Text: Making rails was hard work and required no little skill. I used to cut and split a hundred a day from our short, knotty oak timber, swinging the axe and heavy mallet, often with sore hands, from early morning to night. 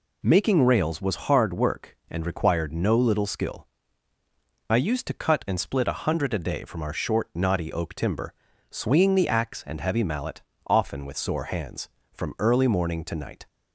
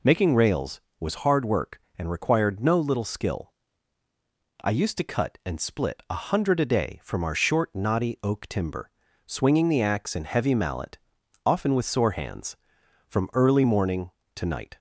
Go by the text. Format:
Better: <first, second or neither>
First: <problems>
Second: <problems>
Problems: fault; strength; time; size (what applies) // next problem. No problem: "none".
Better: neither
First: none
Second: none